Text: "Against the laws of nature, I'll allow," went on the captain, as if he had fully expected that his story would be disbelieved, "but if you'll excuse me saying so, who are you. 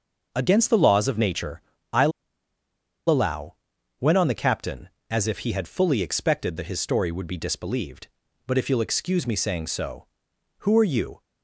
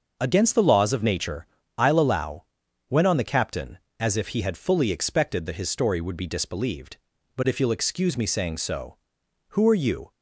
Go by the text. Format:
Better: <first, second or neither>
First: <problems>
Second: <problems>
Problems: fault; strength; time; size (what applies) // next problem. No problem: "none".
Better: second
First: starts louder than the rest; until 1.3 s; 6 dB // pauses between "I'll" and "allow"; at 2.1 s; 0.98 s long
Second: starts louder than the rest; until 1.2 s; 6 dB